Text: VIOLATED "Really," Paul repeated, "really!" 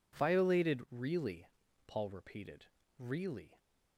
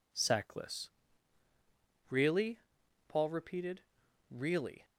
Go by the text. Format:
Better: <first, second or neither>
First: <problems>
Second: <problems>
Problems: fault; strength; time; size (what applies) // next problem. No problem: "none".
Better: first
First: none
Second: says "Sackless" for "VIOLATED"; at 0.1 s